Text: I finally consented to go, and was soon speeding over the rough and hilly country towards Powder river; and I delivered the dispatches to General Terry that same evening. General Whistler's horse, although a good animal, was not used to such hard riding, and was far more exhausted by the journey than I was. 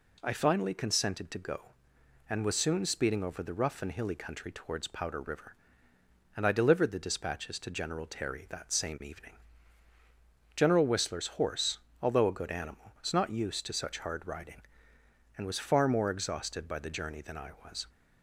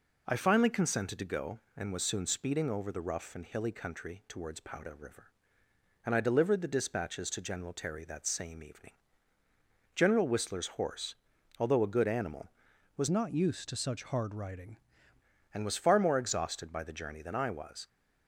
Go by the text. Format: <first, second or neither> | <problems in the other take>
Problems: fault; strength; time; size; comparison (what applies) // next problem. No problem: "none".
first | changes voice from "not" to "riding"; from 13.1 to 14.7 s; 1.6 s long